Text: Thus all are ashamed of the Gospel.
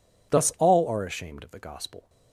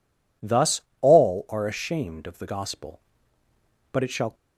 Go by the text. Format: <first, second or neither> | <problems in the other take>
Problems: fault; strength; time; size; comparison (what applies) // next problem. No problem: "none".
first | pauses between "Thus" and "all"; slight; at 0.8 s; 0.18 s long // goes on to say "But it shall"; slight; from 3.9 s on; 0.42 s long